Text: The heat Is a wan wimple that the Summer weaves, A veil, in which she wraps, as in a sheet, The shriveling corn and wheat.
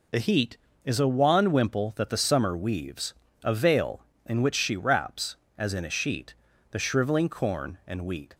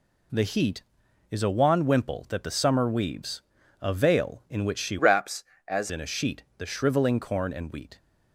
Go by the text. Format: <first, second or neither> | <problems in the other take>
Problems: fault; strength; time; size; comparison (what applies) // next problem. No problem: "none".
first | changes voice from "wraps" to "as"; from 4.9 to 5.9 s; 1.0 s long